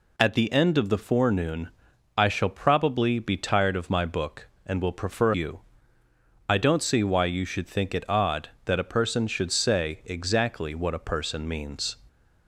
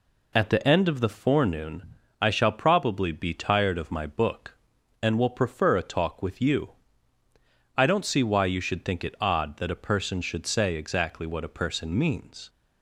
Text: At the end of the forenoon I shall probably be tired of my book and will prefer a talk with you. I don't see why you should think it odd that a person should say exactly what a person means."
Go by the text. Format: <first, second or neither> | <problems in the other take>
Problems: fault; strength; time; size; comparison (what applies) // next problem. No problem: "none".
second | pauses between "forenoon" and "I"; noticeable; at 1.6 s; 0.48 s long; slight in the second // skips "a talk with"; at 5.3 s